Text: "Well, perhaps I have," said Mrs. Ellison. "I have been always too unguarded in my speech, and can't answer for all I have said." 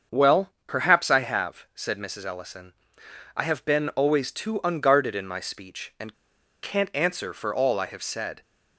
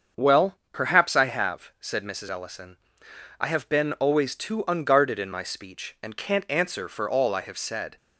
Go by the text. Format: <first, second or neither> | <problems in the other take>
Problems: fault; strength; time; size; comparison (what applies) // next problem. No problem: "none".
second | starts louder than the rest; until 1.2 s; 6.5 dB; also in the second // pauses between "and" and "can't"; noticeable; at 6.1 s; 0.48 s long